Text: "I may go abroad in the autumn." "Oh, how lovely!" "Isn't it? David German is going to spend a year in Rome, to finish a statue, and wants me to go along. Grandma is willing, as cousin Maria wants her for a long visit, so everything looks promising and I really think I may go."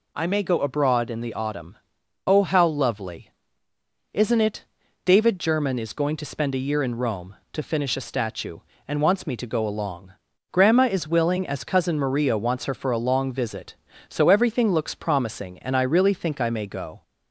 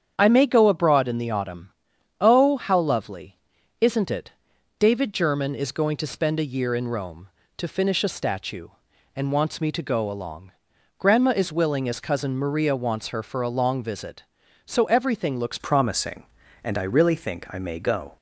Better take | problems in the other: first | starts louder than the rest; strong; until 1.1 s; 8 dB // changes voice at "promising"; from 15.5 s on; 2.6 s long

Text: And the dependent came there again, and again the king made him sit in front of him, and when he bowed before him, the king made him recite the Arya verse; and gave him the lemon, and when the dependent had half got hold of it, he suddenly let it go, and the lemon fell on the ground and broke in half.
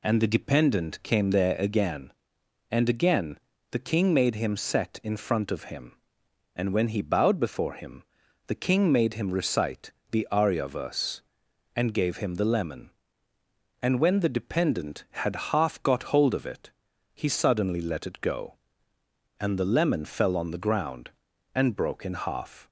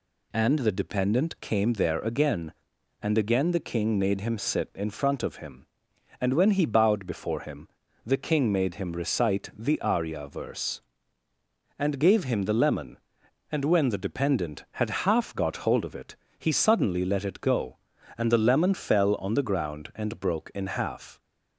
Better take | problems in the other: second | pauses between "again" and "the"; slight; at 3.3 s; 0.34 s long // says "set" for "sit"; at 4.5 s // pauses between "recite" and "the"; slight; at 9.9 s; 0.20 s long

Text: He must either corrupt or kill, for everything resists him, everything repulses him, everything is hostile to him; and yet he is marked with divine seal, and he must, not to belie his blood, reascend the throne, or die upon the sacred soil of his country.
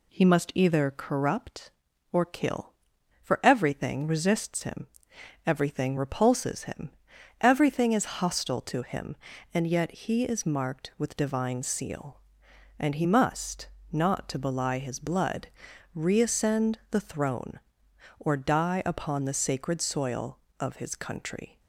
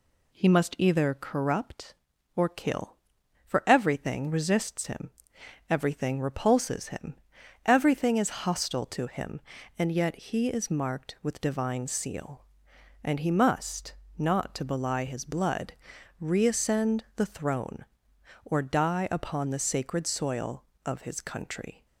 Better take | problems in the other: neither | none

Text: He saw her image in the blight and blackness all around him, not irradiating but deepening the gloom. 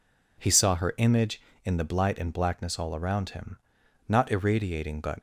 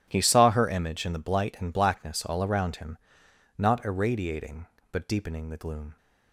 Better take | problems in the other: second | stops before "deepening the gloom"; at 5.1 s

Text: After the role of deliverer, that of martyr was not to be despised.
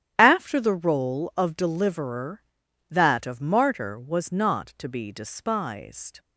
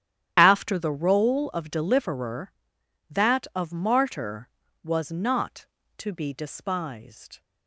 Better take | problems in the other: neither | starts louder than the rest; strong; the same in both

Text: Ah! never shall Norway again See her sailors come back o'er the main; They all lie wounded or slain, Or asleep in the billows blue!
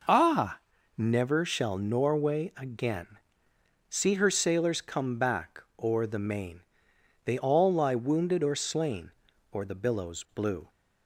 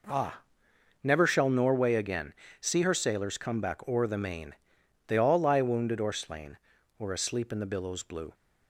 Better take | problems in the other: second | pauses between "again" and "See"; noticeable; at 3.1 s; 0.70 s long; slight in the second // pauses between "back" and "o'er"; slight; at 5.6 s; 0.18 s long // skips "asleep in"; at 9.6 s

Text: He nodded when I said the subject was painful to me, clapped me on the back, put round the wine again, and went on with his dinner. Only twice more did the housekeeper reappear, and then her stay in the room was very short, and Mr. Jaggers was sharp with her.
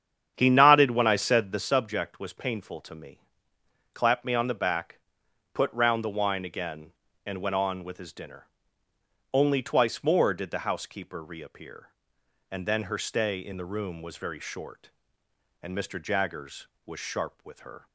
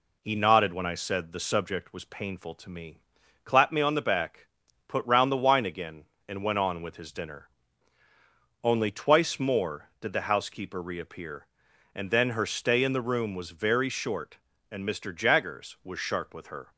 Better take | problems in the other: second | starts louder than the rest; strong; until 1.7 s; 8.5 dB

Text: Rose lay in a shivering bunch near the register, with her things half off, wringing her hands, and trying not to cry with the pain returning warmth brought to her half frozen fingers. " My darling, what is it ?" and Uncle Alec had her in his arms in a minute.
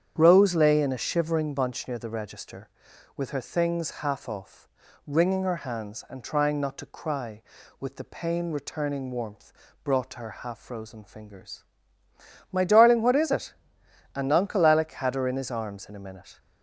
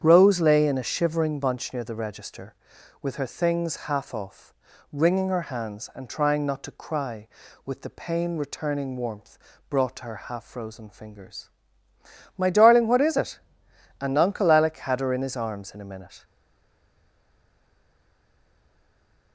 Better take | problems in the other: first | starts louder than the rest; strong; until 1.0 s; 8.5 dB; strong in the first // pauses between "warmth" and "brought"; slight; at 9.3 s; 0.32 s long; slight in the first // stays silent after the last word; strong; from 16.2 s on; 3.1 s long

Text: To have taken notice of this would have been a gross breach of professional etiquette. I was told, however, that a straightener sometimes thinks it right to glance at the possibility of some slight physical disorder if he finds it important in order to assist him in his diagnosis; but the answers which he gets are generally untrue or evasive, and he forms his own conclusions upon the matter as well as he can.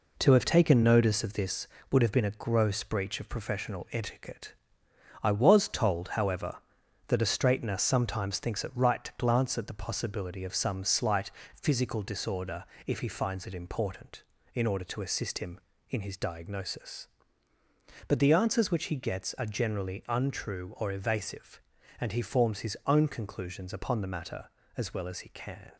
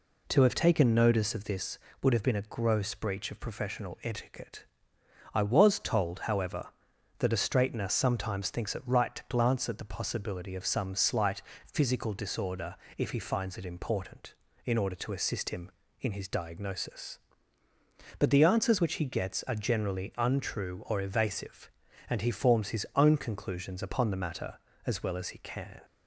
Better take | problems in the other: second | gets quieter; noticeable; throughout; 6 dB // pauses between "slight" and "physical"; slight; at 11.2 s; 0.32 s long; slight in the second // pauses between "disorder" and "if"; slight; at 12.6 s; 0.22 s long; slight in the second

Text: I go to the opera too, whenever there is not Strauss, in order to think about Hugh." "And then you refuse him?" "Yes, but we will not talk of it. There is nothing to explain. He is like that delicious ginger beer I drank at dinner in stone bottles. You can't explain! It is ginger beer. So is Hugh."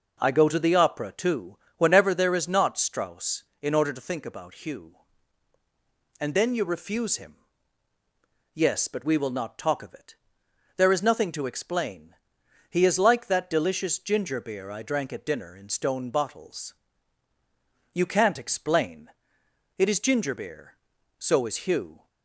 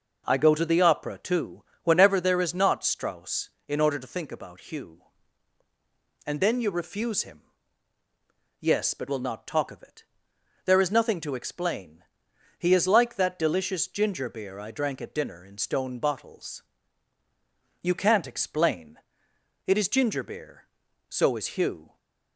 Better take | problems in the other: first | skips "we"; at 9.0 s

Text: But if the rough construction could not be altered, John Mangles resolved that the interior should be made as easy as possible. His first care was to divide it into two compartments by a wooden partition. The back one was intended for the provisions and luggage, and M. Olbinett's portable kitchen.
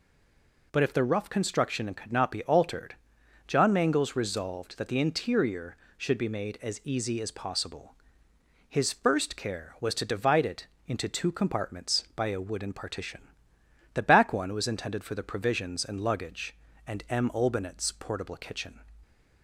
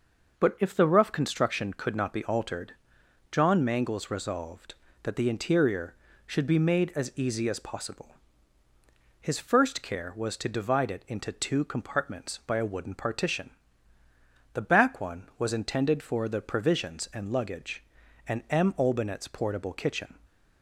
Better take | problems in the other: second | stays silent before the first word; slight; until 0.7 s; 0.7 s long // pauses between "it" and "into"; slight; at 10.6 s; 0.18 s long

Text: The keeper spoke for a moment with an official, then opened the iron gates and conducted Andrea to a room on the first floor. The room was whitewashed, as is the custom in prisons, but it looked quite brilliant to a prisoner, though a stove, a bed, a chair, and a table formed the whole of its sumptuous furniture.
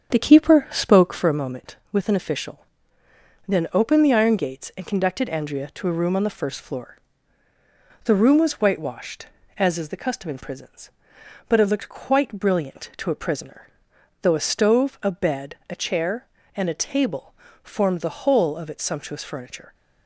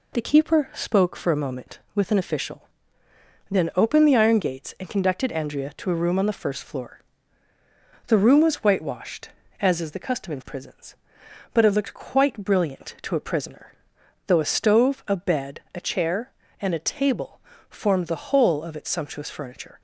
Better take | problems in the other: second | starts louder than the rest; strong; until 1.4 s; 7.5 dB // pauses between "table" and "formed"; slight; at 17.3 s; 0.30 s long; slight in the second

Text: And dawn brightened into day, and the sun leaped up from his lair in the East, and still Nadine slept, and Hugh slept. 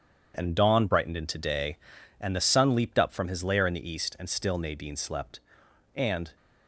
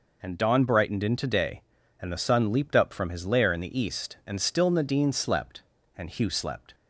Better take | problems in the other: second | stops before "Hugh slept"; at 6.3 s

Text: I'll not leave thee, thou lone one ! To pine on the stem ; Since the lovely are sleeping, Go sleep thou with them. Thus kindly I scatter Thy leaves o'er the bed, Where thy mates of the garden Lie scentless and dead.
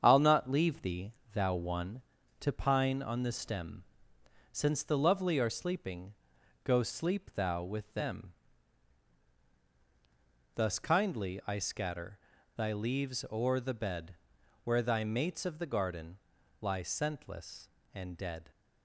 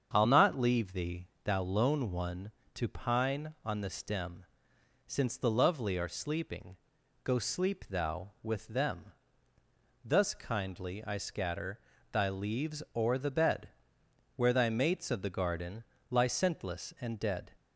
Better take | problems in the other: second | starts louder than the rest; strong; until 1.0 s; 7.5 dB; strong in the second // skips "lone"; at 1.5 s // pauses between "scatter" and "Thy"; at 12.1 s; 0.38 s long; slight in the second // pauses between "garden" and "Lie"; at 16.1 s; 0.42 s long; slight in the second

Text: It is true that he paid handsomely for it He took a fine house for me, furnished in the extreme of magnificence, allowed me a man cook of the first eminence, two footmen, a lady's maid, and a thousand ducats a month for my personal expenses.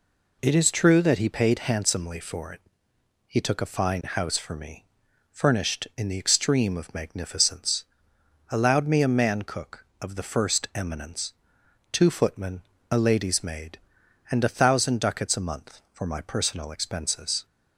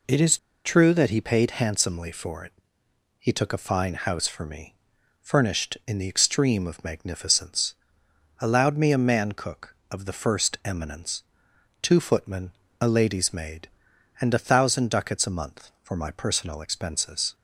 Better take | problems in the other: first | pauses between "is" and "true"; slight; at 0.3 s; 0.28 s long // pauses between "it" and "He"; noticeable; at 2.5 s; 0.66 s long; noticeable in the first

